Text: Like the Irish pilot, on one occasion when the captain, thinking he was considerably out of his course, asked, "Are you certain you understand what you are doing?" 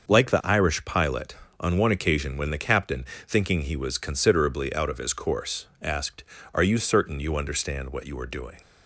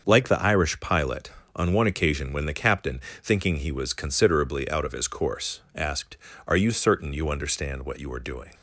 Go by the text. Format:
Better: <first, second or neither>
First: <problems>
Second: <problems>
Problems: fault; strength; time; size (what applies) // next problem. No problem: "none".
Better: neither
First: starts louder than the rest; until 1.1 s; 6.5 dB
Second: starts louder than the rest; until 1.0 s; 6.5 dB